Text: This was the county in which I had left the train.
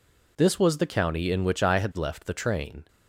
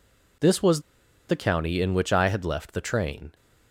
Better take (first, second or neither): first